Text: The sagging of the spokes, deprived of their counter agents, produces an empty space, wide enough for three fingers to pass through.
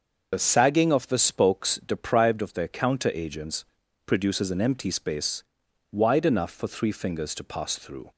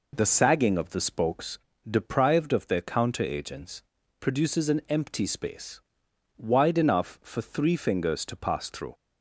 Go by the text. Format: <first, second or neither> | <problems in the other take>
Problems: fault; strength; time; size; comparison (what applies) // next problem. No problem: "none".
second | loses the start of "The"; at 0.3 s; 55 ms // starts louder than the rest; until 1.3 s; 6 dB